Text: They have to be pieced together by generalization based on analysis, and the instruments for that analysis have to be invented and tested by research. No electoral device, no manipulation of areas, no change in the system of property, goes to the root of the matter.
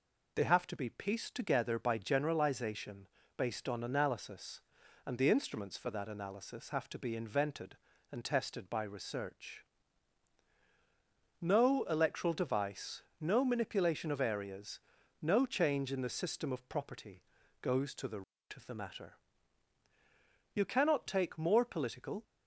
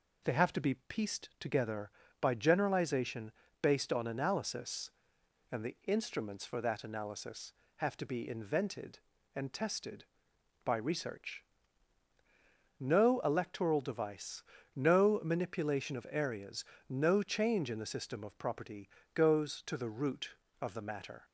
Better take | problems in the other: second | pauses between "generalization" and "based"; slight; at 3.0 s; 0.30 s long; slight in the second // goes on to say "You cannot take more political"; strong; from 20.5 s on; 1.7 s long

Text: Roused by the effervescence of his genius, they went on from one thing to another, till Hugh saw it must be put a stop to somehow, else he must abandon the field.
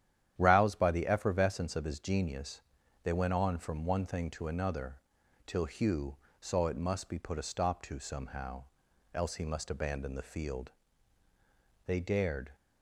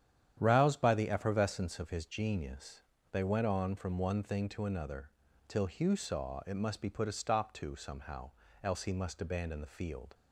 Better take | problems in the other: second | starts louder than the rest; strong; until 1.3 s; 10.5 dB; strong in the second // pauses between "Hugh" and "saw"; slight; at 6.1 s; 0.24 s long // goes on to say "They dared"; noticeable; from 11.8 s on; 0.68 s long

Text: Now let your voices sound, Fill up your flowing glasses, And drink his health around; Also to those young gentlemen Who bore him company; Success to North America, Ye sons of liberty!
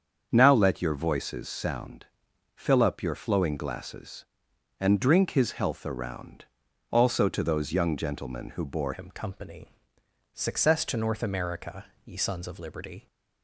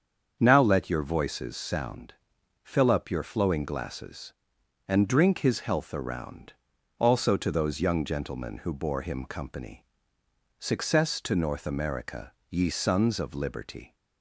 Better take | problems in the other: second | starts louder than the rest; strong; until 1.3 s; 7 dB; strong in the second // changes voice at "him"; from 8.9 s on; 4.1 s long

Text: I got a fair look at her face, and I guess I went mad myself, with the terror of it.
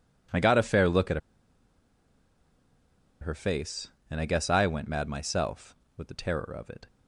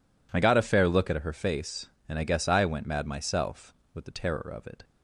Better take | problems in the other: second | pauses between "at" and "her"; strong; at 1.1 s; 2.0 s long

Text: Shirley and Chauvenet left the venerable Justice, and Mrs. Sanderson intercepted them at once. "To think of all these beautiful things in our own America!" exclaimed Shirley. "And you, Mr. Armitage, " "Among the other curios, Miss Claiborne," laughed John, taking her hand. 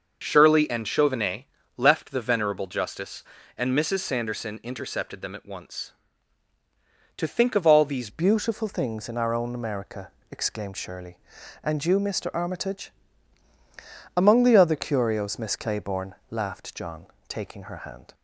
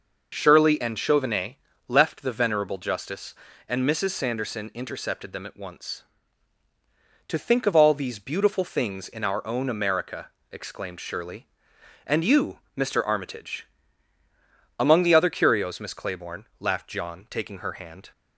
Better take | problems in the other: second | starts louder than the rest; until 1.2 s; 6 dB // pauses between "Chauvenet" and "left"; slight; at 1.4 s; 0.30 s long; slight in the second // changes voice at "beautiful"; from 8.0 s on; 10.1 s long

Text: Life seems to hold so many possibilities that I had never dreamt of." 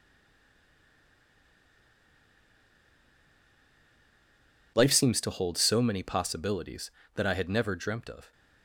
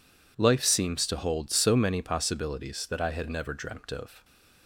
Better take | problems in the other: second | stays silent before the first word; strong; until 4.7 s; 4.7 s long

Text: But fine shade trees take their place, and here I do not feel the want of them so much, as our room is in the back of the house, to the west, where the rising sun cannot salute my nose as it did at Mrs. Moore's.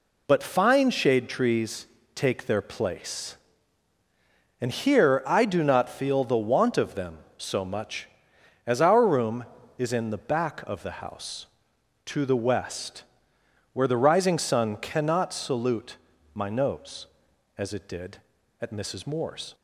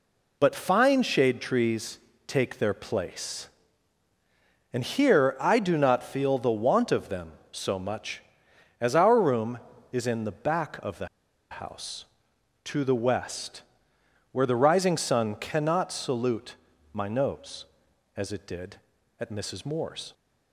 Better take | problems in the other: first | pauses between "trees" and "take"; slight; at 1.9 s; 0.28 s long; slight in the first // pauses between "the" and "house"; at 11.0 s; 0.44 s long // pauses between "salute" and "my"; at 16.5 s; 0.38 s long; also in the first

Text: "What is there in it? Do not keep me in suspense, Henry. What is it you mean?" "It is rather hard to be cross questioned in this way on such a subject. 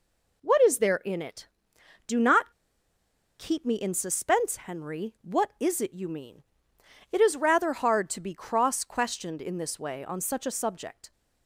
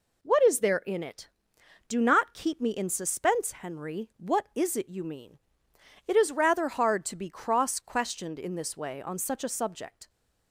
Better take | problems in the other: second | pauses between "not" and "keep"; noticeable; at 2.5 s; 0.87 s long

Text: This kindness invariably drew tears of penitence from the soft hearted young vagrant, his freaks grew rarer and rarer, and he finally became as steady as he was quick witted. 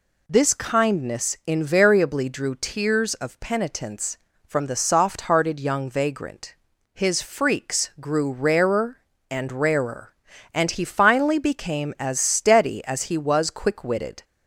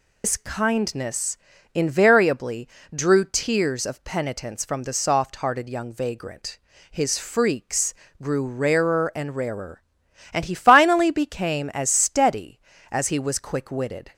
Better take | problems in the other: first | loses the start of "This"; at 0.2 s; 115 ms // pauses between "kindness" and "invariably"; at 1.3 s; 0.38 s long // pauses between "invariably" and "drew"; slight; at 2.6 s; 0.28 s long // pauses between "freaks" and "grew"; slight; at 7.9 s; 0.28 s long

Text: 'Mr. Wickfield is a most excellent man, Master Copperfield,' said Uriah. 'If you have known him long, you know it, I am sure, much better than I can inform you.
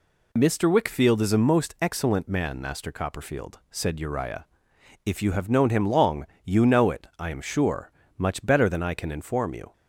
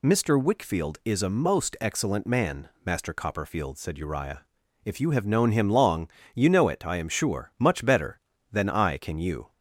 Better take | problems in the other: first | skips "inform"; at 9.1 s

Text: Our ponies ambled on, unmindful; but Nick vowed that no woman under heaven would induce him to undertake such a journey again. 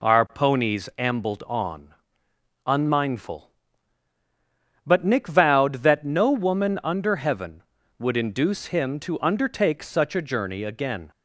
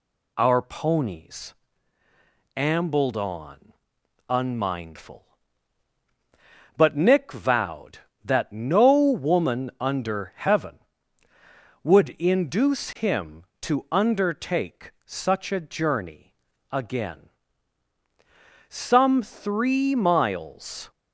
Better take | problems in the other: first | pauses between "ponies" and "ambled"; at 1.5 s; 1.0 s long // pauses between "undertake" and "such"; slight; at 14.9 s; 0.16 s long // pauses between "journey" and "again"; slight; at 16.3 s; 0.24 s long // goes on to say "Some three miles"; strong; from 18.6 s on; 2.2 s long

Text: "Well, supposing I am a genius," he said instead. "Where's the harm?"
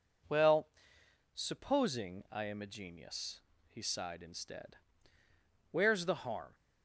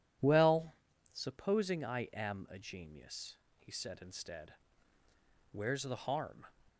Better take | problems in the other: second | says "sighed" for "said"; at 3.8 s

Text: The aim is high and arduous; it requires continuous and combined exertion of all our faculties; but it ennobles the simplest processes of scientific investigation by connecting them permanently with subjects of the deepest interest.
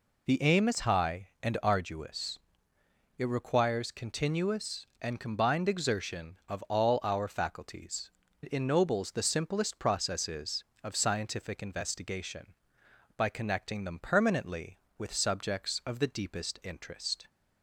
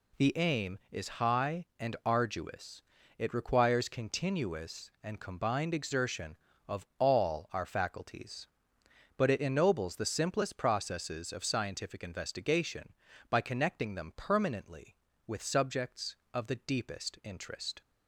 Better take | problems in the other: second | skips "but"; at 8.2 s

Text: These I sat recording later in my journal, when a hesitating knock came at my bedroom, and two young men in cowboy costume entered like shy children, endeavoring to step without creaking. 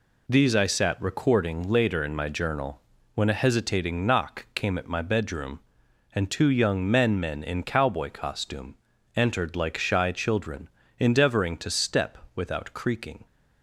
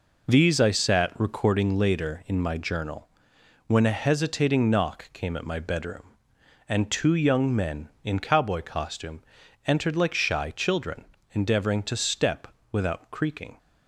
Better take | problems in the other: second | says "men" twice; at 7.1 s // pauses between "costume" and "entered"; at 8.7 s; 0.42 s long; noticeable in the second // pauses between "step" and "without"; slight; at 12.1 s; 0.18 s long; slight in the second

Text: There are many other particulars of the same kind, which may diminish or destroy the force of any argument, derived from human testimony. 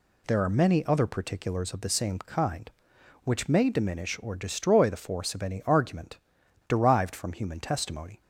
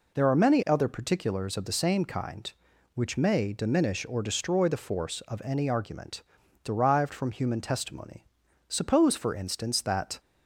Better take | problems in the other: first | goes on to say "Suppose for instance that"; from 8.6 s on; 1.5 s long

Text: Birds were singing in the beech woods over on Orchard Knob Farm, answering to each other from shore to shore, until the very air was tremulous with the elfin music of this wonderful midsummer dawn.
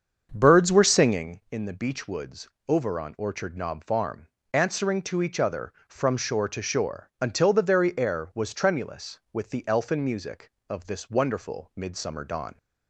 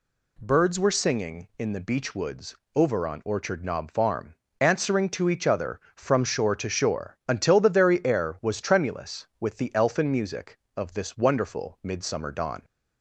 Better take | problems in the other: second | starts louder than the rest; until 1.4 s; 7 dB // pauses between "woods" and "over"; slight; at 2.4 s; 0.20 s long; slight in the second

